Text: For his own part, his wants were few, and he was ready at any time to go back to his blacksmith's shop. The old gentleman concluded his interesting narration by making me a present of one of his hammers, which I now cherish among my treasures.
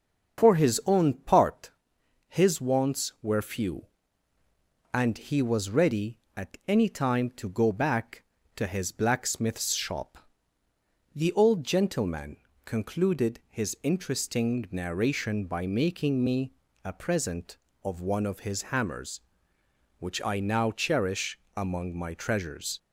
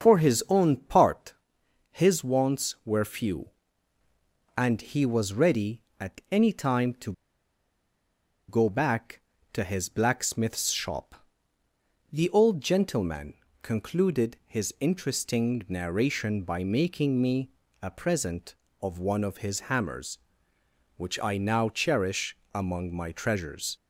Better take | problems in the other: first | starts louder than the rest; until 1.0 s; 6.5 dB; also in the first // pauses between "to" and "go"; strong; at 7.1 s; 1.3 s long // pauses between "gentleman" and "concluded"; slight; at 13.3 s; 0.28 s long; slight in the first // pauses between "me" and "a"; slight; at 17.4 s; 0.32 s long; slight in the first // pauses between "cherish" and "among"; slight; at 22.3 s; 0.16 s long; slight in the first

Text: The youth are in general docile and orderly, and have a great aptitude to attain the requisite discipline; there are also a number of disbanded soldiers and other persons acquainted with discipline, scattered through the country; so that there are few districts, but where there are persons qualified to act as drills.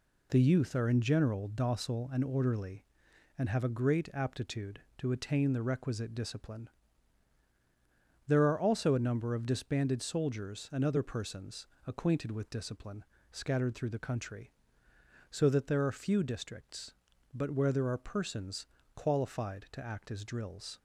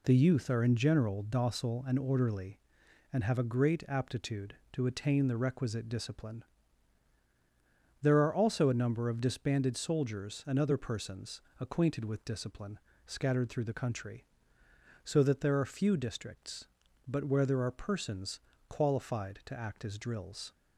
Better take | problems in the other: neither | pauses between "persons" and "acquainted"; slight; the same in both // pauses between "persons" and "qualified"; slight; the same in both

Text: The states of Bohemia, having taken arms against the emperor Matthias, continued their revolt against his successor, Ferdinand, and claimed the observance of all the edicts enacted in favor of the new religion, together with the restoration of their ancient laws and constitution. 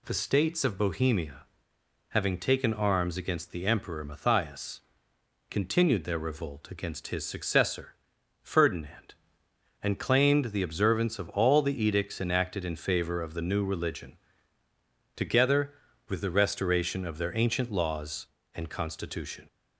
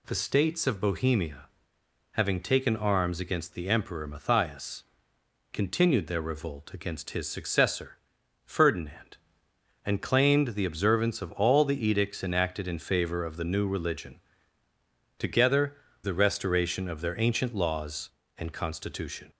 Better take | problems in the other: first | skips "with"; at 15.8 s

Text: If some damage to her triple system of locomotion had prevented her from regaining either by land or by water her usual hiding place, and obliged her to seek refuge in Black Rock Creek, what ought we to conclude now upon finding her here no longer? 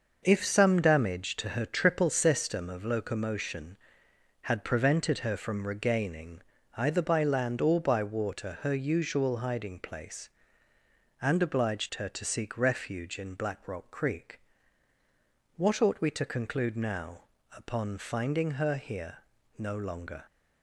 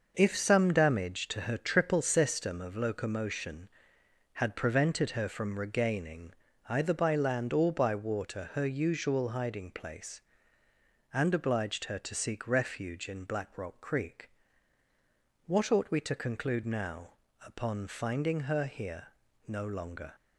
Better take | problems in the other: neither | pauses between "regaining" and "either"; slight; the same in both // pauses between "now" and "upon"; slight; the same in both // pauses between "here" and "no"; the same in both

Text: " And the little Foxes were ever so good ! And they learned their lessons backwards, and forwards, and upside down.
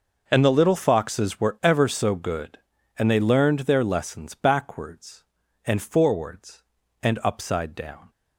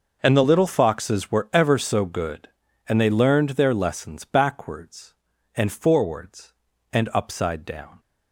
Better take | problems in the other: neither | none

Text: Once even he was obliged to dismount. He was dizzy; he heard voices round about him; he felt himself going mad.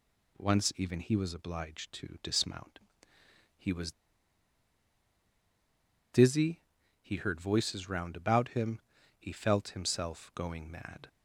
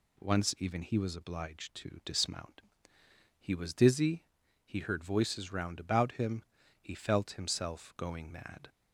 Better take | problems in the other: second | pauses between "was" and "dizzy"; strong; at 3.9 s; 2.2 s long

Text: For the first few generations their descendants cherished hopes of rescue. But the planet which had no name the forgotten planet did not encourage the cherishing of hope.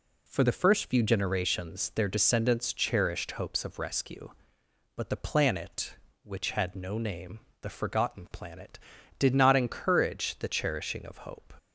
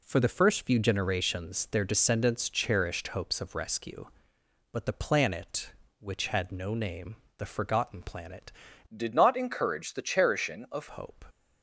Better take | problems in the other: first | pauses between "name" and "the"; slight; at 7.1 s; 0.22 s long; slight in the first // changes voice from "did" to "of"; from 8.9 to 10.8 s; 1.9 s long

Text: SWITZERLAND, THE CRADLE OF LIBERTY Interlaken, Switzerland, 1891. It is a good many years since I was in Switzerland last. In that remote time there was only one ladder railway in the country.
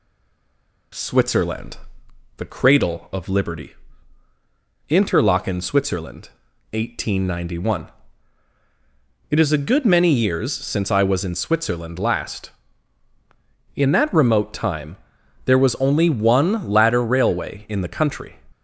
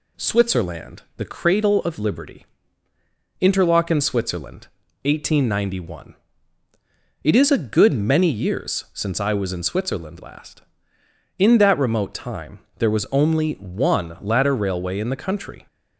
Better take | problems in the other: second | stays silent before the first word; slight; until 0.9 s; 0.9 s long // pauses between "LIBERTY" and "Interlaken"; at 3.7 s; 1.1 s long; noticeable in the second // pauses between "time" and "there"; noticeable; at 14.9 s; 0.48 s long; slight in the second

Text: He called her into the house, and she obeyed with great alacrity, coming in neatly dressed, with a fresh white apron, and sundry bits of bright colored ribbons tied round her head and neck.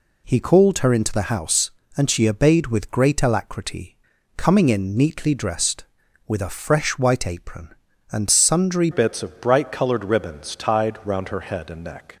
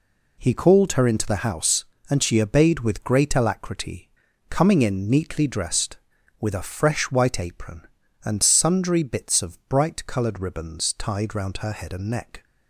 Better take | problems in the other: second | changes voice at "bits"; from 8.9 s on; 3.2 s long

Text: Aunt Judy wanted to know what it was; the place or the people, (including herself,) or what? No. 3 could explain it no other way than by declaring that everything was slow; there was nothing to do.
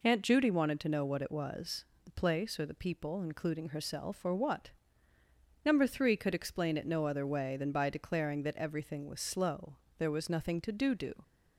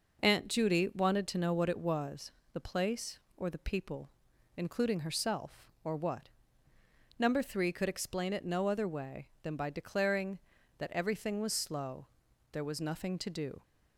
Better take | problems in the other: second | says "do" twice; at 10.9 s

